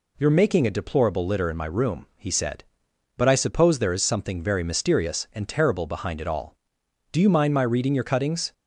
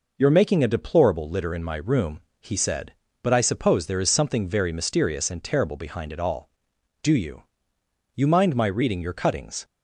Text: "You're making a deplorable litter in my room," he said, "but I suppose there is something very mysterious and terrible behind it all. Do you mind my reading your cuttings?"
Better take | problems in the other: first | says "you" twice; at 8.1 s

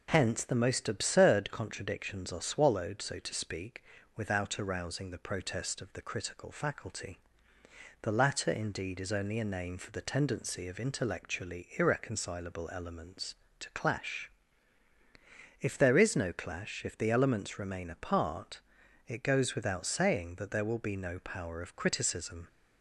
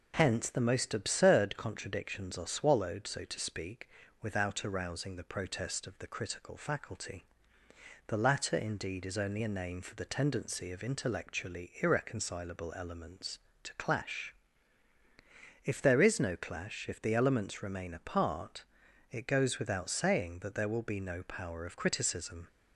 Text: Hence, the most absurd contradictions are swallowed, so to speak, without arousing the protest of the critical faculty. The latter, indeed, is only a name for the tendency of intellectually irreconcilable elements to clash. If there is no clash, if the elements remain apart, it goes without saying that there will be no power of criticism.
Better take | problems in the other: neither | none

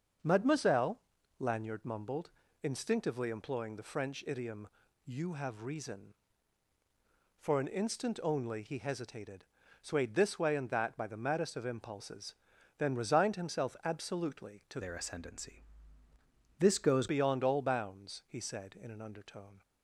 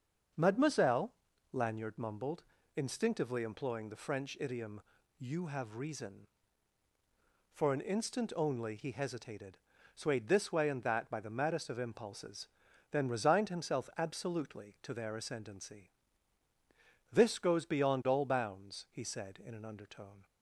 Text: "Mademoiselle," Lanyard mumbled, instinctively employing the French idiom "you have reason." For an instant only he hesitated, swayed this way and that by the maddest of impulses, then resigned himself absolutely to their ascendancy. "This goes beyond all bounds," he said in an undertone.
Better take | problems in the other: second | starts louder than the rest; until 1.6 s; 6.5 dB; also in the second // pauses between "idiom" and "you"; at 4.6 s; 0.38 s long; also in the second // changes voice from "their" to "goes"; from 14.8 to 17.0 s; 2.2 s long

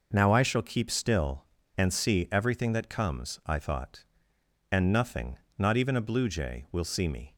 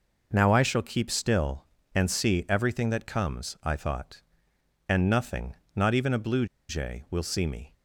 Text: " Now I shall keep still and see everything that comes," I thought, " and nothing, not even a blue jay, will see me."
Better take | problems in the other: first | pauses between "blue" and "jay"; slight; at 6.4 s; 0.23 s long

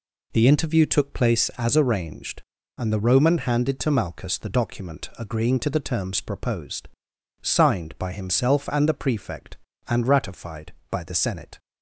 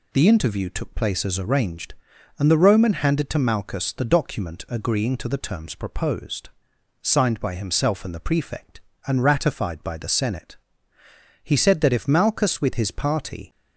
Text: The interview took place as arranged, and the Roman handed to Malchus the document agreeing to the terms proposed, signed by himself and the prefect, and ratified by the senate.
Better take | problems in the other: first | goes on to say "He said that if Malchus with his party"; strong; from 11.4 s on; 2.0 s long

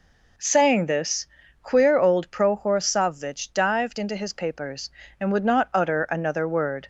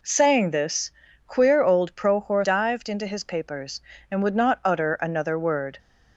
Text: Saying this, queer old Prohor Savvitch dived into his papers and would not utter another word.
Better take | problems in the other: first | skips "Savvitch"; at 2.4 s

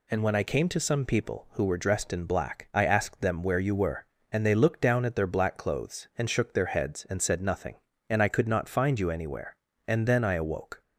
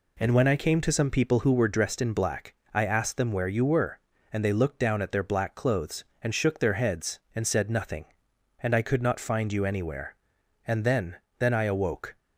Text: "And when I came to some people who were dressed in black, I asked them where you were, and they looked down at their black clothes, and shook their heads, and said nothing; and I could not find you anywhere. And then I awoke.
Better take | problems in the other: first | says "then" twice; at 11.3 s

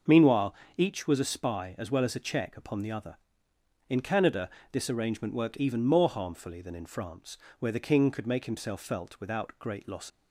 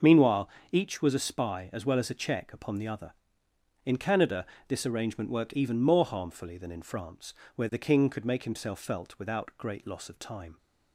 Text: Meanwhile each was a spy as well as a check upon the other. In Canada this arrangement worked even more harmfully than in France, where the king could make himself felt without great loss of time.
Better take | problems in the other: second | starts louder than the rest; until 1.2 s; 6 dB; also in the second // pauses between "Meanwhile" and "each"; slight; at 0.5 s; 0.22 s long; slight in the second // pauses between "Canada" and "this"; slight; at 4.4 s; 0.22 s long; slight in the second // stops before "of time"; at 10.1 s

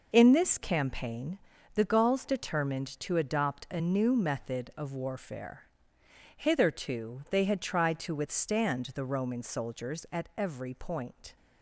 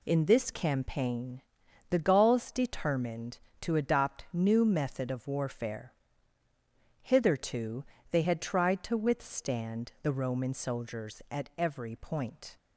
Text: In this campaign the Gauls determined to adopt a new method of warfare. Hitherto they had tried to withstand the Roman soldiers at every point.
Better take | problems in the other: first | pauses between "campaign" and "the"; noticeable; at 1.4 s; 0.50 s long; slight in the first // skips "a"; at 4.2 s // pauses between "Hitherto" and "they"; slight; at 7.8 s; 0.26 s long

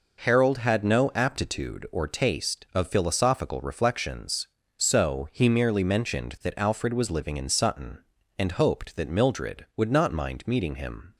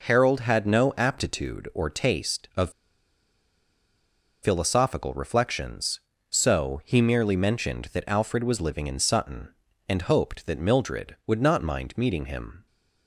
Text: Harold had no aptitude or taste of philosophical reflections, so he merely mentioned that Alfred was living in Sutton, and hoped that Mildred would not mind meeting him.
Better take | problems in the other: first | pauses between "of" and "philosophical"; strong; at 2.7 s; 1.7 s long

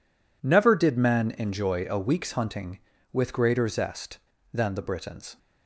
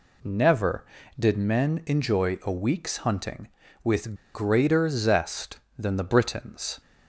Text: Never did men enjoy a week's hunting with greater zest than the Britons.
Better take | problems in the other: first | pauses between "with" and "greater"; slight; at 4.1 s; 0.20 s long

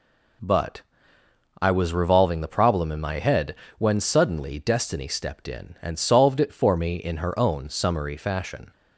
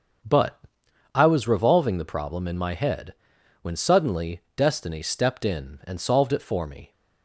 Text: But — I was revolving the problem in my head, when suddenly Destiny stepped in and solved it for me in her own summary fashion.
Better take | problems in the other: first | starts louder than the rest; until 1.7 s; 7 dB // pauses between "suddenly" and "Destiny"; slight; at 4.3 s; 0.16 s long // stops before "in her own summary fashion"; at 6.9 s

